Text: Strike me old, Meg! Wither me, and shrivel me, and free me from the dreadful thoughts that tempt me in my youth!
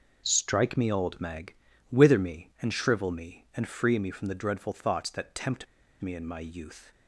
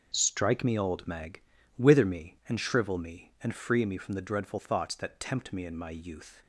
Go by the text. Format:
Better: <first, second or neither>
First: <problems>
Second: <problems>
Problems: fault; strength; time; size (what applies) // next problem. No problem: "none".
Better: second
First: pauses between "tempt" and "me"; at 5.6 s; 0.37 s long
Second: none